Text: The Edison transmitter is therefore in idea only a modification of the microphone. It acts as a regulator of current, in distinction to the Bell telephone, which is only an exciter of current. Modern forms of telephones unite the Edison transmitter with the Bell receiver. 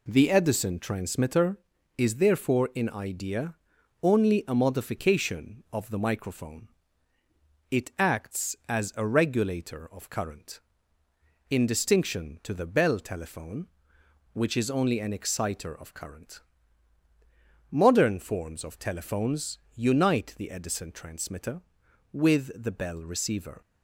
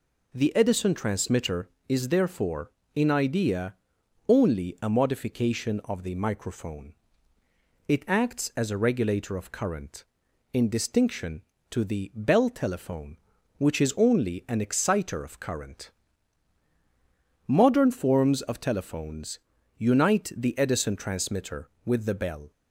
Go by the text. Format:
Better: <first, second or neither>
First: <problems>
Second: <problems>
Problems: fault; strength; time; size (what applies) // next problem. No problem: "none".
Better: first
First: pauses between "idea" and "only"; noticeable; at 3.5 s; 0.46 s long // pauses between "telephones" and "unite"; slight; at 19.5 s; 0.16 s long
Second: pauses between "idea" and "only"; noticeable; at 3.7 s; 0.52 s long // pauses between "telephones" and "unite"; at 19.3 s; 0.40 s long // stops before "receiver"; at 22.5 s